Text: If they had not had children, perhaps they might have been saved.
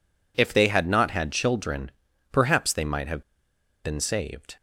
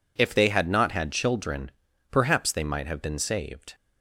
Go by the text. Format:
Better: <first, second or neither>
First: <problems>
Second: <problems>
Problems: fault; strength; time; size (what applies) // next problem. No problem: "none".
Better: second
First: pauses between "have" and "been"; noticeable; at 3.2 s; 0.62 s long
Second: none